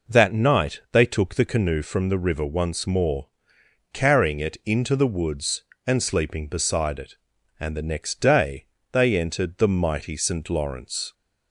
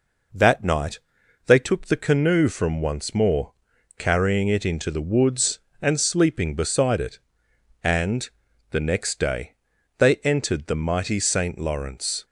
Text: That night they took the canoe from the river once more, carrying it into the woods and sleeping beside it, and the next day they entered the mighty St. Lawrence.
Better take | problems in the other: first | pauses between "night" and "they"; noticeable; at 0.9 s; 0.48 s long // skips "the river"; at 2.8 s // pauses between "and" and "the"; at 8.2 s; 0.42 s long // pauses between "day" and "they"; at 9.5 s; 0.44 s long; slight in the first

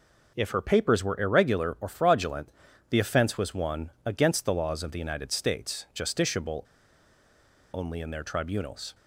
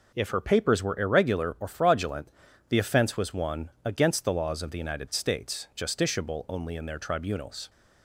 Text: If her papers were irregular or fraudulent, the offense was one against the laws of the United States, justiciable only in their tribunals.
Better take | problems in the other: second | pauses between "justiciable" and "only"; at 6.6 s; 1.0 s long

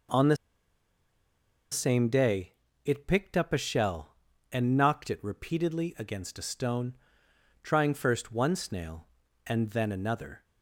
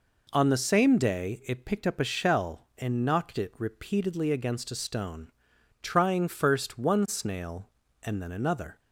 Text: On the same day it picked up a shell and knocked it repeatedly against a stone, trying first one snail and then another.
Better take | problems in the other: second | pauses between "the" and "same"; strong; at 0.3 s; 1.3 s long // pauses between "day" and "it"; slight; at 2.5 s; 0.32 s long

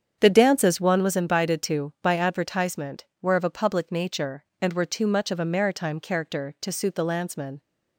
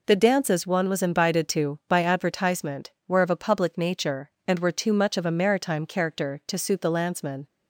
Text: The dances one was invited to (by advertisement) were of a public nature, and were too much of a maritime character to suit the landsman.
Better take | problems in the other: second | starts louder than the rest; strong; until 1.2 s; 8 dB

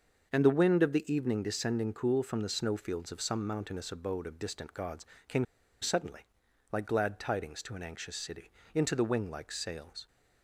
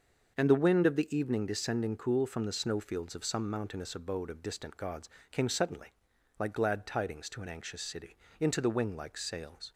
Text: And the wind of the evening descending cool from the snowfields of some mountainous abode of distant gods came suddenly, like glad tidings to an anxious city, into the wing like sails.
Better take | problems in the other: second | starts louder than the rest; until 1.3 s; 6.5 dB; also in the second // pauses between "gods" and "came"; slight; at 5.0 s; 0.20 s long; slight in the second // pauses between "came" and "suddenly"; at 5.4 s; 0.37 s long

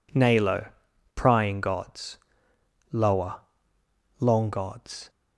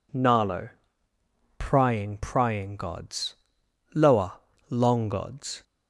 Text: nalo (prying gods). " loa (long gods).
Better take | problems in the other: first | says "prying" twice; at 2.1 s

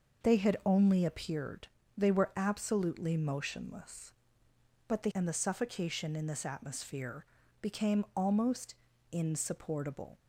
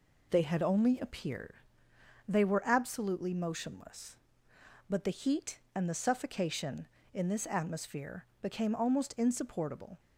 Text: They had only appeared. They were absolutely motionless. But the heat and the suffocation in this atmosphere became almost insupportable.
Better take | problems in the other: second | skips "heat"; at 5.1 s // pauses between "atmosphere" and "became"; slight; at 7.2 s; 0.36 s long; slight in the second // pauses between "almost" and "insupportable"; slight; at 8.7 s; 0.36 s long

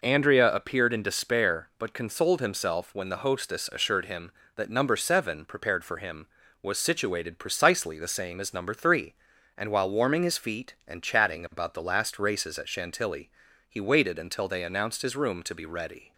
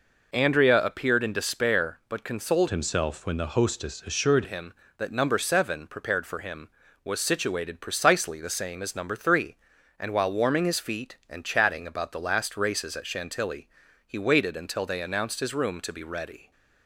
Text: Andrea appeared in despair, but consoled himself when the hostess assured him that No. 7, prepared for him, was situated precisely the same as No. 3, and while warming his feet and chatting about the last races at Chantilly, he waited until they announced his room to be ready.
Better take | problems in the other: first | changes voice from "himself" to "assured"; from 2.6 to 4.4 s; 1.8 s long

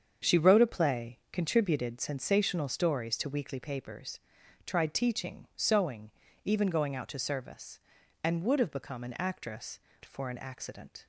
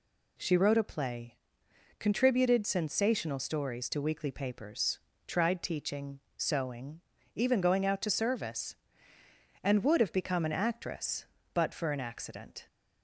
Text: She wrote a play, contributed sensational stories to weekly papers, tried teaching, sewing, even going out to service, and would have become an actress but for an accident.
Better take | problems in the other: second | starts louder than the rest; strong; until 1.3 s; 7.5 dB // skips "but"; at 9.9 s

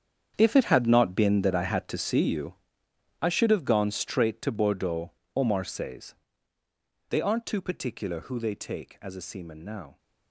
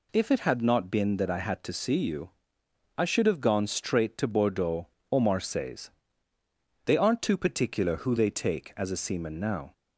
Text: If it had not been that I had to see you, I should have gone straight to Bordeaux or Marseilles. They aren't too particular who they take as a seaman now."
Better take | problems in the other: second | gets quieter; strong; throughout; 14 dB

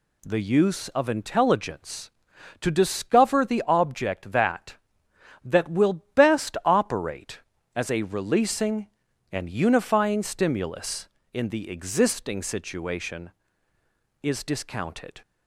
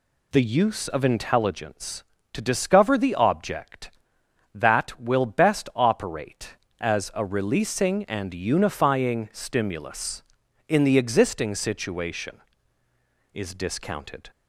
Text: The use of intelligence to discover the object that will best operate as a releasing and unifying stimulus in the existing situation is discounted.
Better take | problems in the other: second | says "that" twice; at 5.4 s

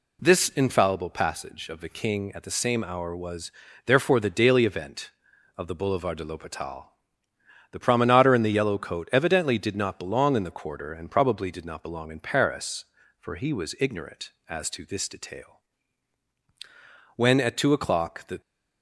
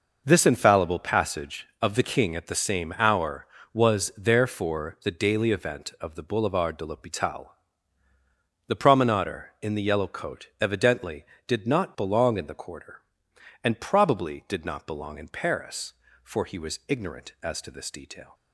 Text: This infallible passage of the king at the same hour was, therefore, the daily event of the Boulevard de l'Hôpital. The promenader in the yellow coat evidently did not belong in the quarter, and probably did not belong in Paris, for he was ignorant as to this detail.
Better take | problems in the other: second | goes on to say "When at two o'clock the"; noticeable; from 17.1 s on; 1.2 s long

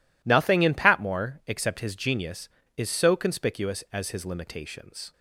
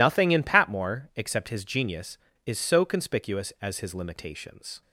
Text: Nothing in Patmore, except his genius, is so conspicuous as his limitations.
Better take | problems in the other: first | loses the start of "Nothing"; at 0.0 s; 70 ms

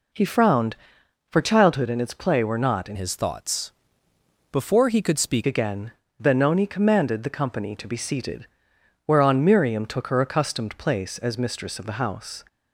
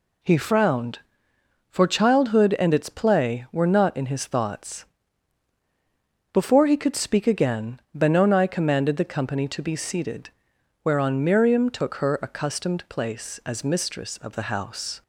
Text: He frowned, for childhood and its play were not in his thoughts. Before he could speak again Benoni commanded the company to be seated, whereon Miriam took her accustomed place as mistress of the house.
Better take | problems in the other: second | changes voice from "his" to "speak"; from 2.9 to 5.4 s; 2.5 s long // pauses between "again" and "Benoni"; slight; at 5.9 s; 0.28 s long

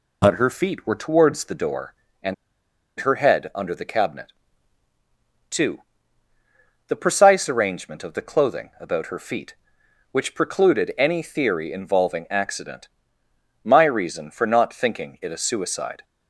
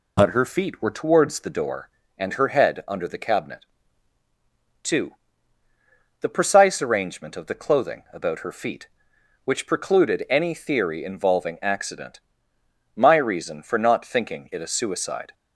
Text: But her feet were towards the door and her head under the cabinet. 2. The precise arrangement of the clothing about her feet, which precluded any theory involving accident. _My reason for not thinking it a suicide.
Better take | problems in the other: second | pauses between "and" and "her"; noticeable; at 2.3 s; 0.64 s long

